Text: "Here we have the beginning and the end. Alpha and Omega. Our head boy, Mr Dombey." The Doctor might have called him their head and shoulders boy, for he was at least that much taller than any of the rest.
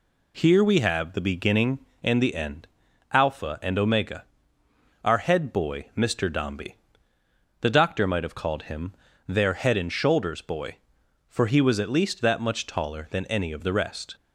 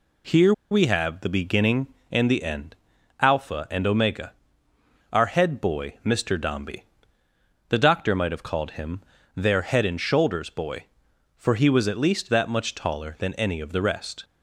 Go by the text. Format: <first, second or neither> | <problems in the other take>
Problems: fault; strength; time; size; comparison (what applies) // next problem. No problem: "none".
first | pauses between "Here" and "we"; slight; at 0.5 s; 0.19 s long // pauses between "him" and "their"; slight; at 9.0 s; 0.34 s long; slight in the first